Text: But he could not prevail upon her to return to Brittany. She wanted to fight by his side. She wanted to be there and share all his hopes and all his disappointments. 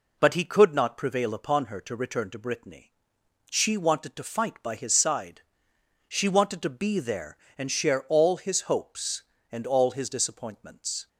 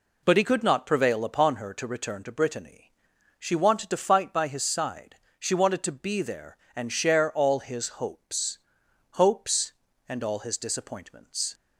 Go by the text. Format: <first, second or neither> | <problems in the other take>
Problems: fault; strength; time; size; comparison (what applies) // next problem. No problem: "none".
first | says "hopes" twice; at 9.1 s